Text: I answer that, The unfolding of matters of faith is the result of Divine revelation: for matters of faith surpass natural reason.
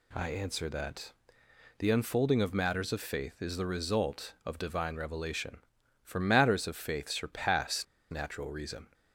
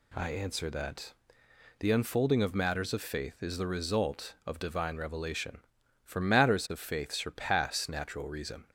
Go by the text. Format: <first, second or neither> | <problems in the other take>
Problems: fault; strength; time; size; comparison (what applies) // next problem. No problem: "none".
second | pauses between "surpass" and "natural"; slight; at 7.8 s; 0.26 s long